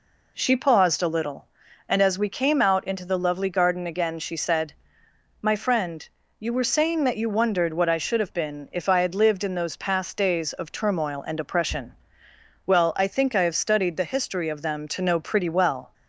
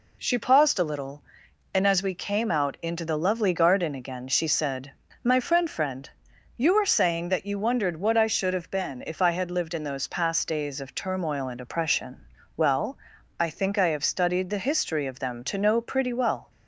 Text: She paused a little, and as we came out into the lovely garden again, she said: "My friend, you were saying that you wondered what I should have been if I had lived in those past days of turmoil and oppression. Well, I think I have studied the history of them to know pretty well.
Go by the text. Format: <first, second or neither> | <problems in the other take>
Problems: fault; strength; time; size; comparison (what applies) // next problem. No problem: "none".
first | says "friend" twice; at 5.6 s